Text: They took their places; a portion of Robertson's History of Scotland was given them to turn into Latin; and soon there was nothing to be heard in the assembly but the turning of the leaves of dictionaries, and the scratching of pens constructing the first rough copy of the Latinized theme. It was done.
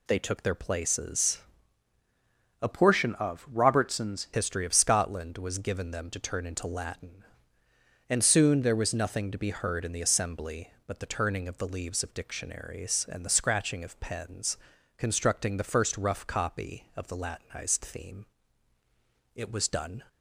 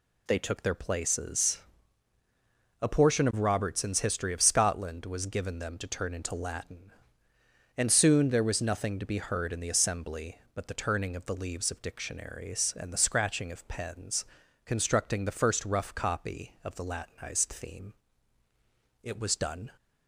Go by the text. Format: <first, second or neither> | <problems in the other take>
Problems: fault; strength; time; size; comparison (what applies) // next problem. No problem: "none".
second | changes voice from "portion" to "Robertson's"; from 2.7 to 4.2 s; 1.5 s long // pauses between "pens" and "constructing"; at 14.5 s; 0.40 s long; also in the second